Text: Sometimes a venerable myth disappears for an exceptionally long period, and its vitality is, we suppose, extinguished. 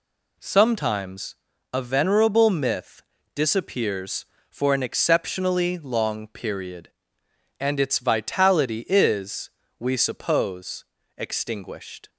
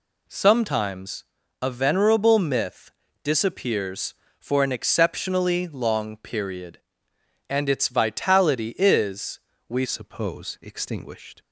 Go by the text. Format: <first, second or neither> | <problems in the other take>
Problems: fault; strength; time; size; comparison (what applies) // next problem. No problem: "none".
first | pauses between "Sometimes" and "a"; at 1.2 s; 0.40 s long; also in the first // pauses between "myth" and "disappears"; slight; at 2.9 s; 0.32 s long; slight in the first // changes voice at "suppose"; from 9.8 s on; 1.6 s long